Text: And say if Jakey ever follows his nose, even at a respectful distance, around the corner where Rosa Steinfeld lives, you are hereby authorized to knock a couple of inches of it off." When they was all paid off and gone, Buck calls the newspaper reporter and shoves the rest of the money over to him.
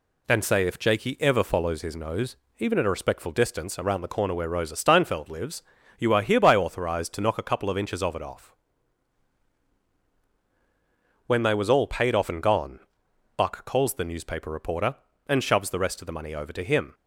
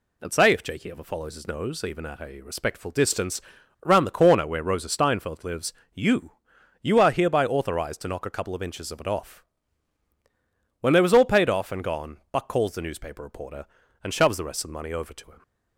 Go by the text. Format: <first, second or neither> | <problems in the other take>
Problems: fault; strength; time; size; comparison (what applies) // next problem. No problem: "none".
first | says "you" twice; at 6.8 s